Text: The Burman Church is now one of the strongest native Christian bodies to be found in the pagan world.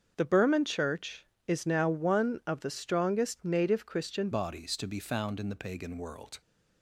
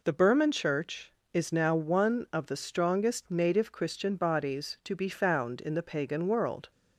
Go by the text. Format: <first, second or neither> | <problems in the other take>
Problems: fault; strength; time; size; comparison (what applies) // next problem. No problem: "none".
second | starts louder than the rest; until 1.1 s; 6.5 dB // changes voice at "bodies"; from 4.3 s on; 2.1 s long